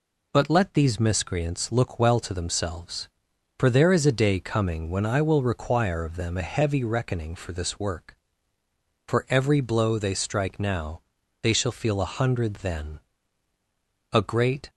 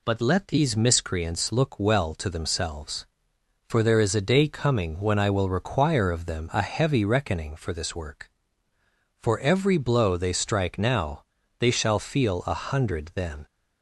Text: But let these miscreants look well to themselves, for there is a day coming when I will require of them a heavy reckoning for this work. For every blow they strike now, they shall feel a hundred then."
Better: second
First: goes on to say "A great"; from 14.1 s on; 0.58 s long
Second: none

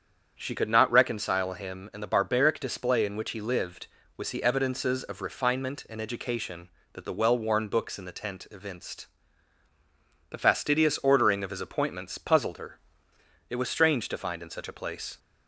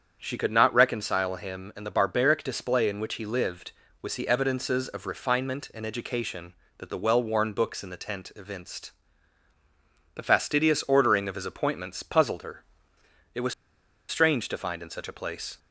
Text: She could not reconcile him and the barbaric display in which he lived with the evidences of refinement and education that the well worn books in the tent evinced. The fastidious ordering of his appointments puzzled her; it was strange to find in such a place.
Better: first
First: starts louder than the rest; strong; until 1.3 s; 7.5 dB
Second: starts louder than the rest; strong; until 1.2 s; 7.5 dB // pauses between "was" and "strange"; noticeable; at 13.5 s; 0.55 s long

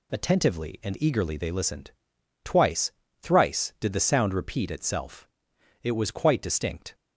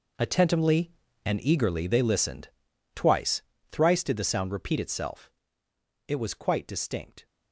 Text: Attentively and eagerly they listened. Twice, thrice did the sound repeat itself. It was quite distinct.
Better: first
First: none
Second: gets quieter; strong; throughout; 13 dB

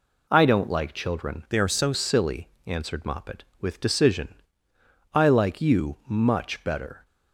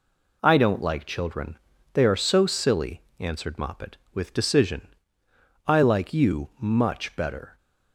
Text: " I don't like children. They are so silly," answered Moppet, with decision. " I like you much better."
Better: second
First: changes voice from "They" to "so"; from 1.5 to 1.9 s; 0.4 s long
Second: none

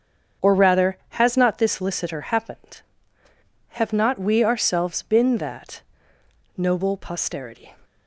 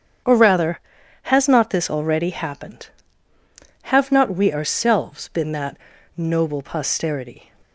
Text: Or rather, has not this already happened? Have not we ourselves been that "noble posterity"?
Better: second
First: starts louder than the rest; strong; until 1.5 s; 7.5 dB // says "licitor" for "already"; at 1.7 s // pauses between "that" and "noble"; noticeable; at 5.8 s; 0.74 s long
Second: starts louder than the rest; strong; until 1.7 s; 8 dB // pauses between "that" and "noble"; at 5.7 s; 0.39 s long

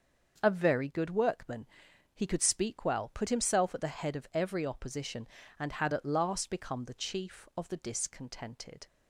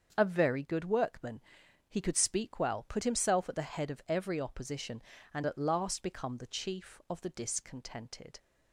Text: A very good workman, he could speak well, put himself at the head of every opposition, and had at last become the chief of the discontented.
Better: first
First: starts louder than the rest; until 1.4 s; 6.5 dB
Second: starts louder than the rest; strong; until 1.1 s; 7 dB // skips "had"; at 5.4 s

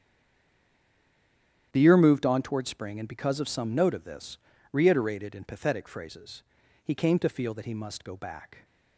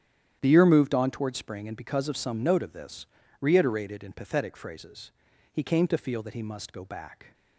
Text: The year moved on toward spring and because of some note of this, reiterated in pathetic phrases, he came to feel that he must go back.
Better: second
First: stays silent before the first word; noticeable; until 1.7 s; 1.7 s long // starts louder than the rest; strong; until 2.7 s; 10 dB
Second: starts louder than the rest; strong; until 1.4 s; 10 dB

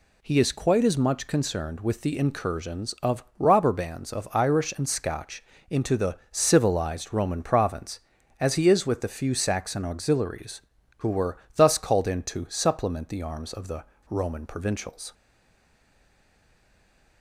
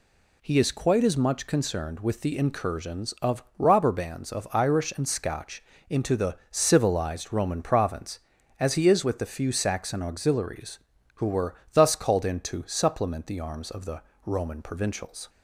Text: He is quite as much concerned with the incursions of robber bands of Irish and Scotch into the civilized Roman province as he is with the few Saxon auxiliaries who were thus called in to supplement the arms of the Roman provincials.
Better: second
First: pauses between "Scotch" and "into"; slight; at 5.4 s; 0.28 s long // pauses between "the" and "civilized"; slight; at 6.1 s; 0.16 s long // pauses between "were" and "thus"; slight; at 11.3 s; 0.18 s long // pauses between "the" and "Roman"; slight; at 13.8 s; 0.25 s long // stays silent after the last word; noticeable; from 15.1 s on; 2.1 s long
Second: pauses between "Scotch" and "into"; slight; at 5.6 s; 0.28 s long // pauses between "the" and "civilized"; slight; at 6.3 s; 0.16 s long // pauses between "were" and "thus"; slight; at 11.5 s; 0.18 s long // pauses between "the" and "Roman"; slight; at 14.0 s; 0.24 s long

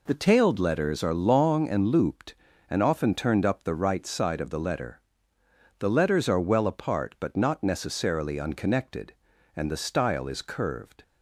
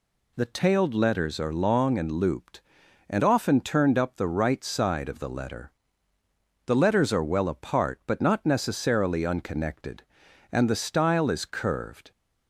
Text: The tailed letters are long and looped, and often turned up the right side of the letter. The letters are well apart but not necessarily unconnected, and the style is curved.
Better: neither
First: none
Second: none

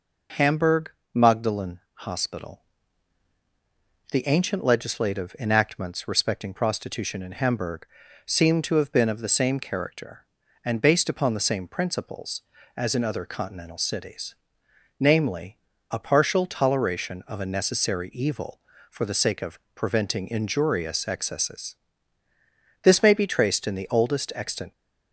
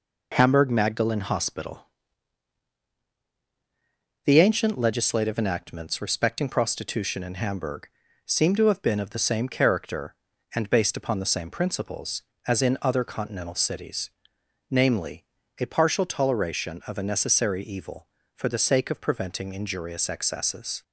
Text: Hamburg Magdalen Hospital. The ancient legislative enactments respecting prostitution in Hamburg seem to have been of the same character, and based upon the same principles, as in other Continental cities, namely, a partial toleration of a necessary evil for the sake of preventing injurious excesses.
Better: second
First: pauses between "Hamburg" and "Magdalen"; slight; at 0.9 s; 0.22 s long // pauses between "Hamburg" and "seem"; at 7.8 s; 0.40 s long // pauses between "of" and "preventing"; slight; at 19.5 s; 0.16 s long // goes on to say "This may be traced in the oldest extant"; strong; from 22.8 s on; 1.8 s long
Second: pauses between "Hamburg" and "seem"; slight; at 7.8 s; 0.36 s long

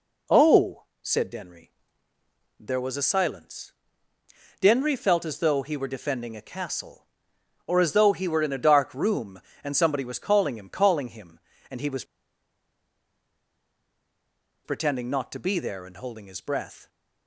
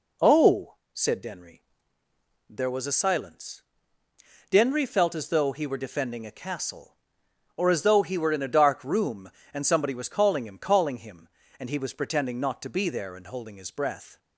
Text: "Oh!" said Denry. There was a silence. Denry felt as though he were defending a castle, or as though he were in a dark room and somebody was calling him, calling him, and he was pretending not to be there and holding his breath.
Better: second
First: pauses between "was" and "pretending"; strong; at 12.0 s; 2.6 s long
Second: none

